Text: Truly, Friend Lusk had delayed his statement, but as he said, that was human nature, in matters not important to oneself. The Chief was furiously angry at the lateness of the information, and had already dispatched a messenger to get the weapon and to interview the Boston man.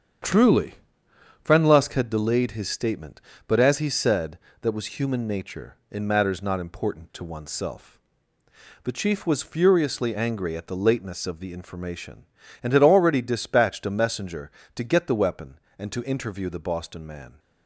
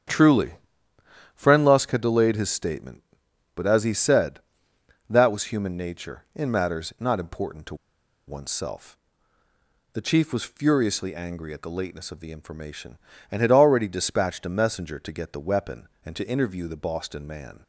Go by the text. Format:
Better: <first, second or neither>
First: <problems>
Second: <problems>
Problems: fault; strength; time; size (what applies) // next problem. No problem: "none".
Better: first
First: starts louder than the rest; strong; until 1.9 s; 8 dB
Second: starts louder than the rest; strong; until 1.8 s; 8 dB // pauses between "to" and "oneself"; noticeable; at 7.7 s; 0.52 s long